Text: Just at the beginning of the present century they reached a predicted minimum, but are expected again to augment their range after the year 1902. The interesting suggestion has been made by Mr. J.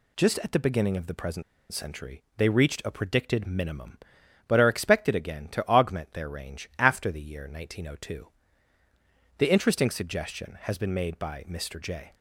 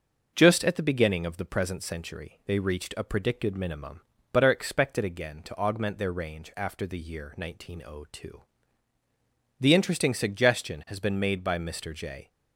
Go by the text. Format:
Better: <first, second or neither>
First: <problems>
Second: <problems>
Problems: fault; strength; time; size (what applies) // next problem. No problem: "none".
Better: second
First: pauses between "present" and "century"; slight; at 1.4 s; 0.28 s long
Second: none